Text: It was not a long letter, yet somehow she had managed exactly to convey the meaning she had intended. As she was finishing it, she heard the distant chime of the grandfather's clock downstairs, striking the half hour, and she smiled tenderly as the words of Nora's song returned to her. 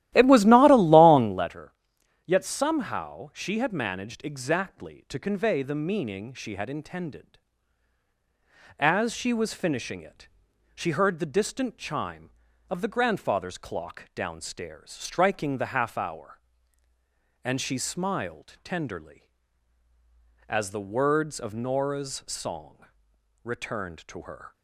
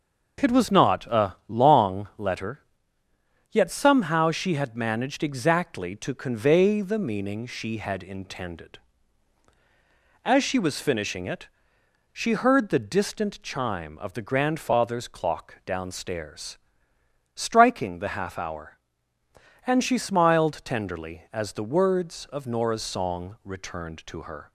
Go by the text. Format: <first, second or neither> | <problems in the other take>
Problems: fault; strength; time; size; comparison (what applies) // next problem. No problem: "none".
second | starts louder than the rest; strong; until 1.5 s; 14.5 dB // pauses between "song" and "returned"; noticeable; at 22.8 s; 0.60 s long